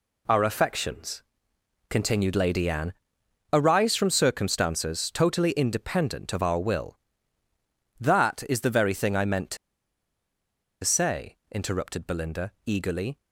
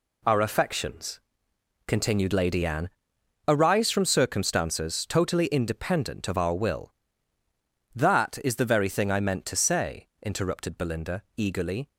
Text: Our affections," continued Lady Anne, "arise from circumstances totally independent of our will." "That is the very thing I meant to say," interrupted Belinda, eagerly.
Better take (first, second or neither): second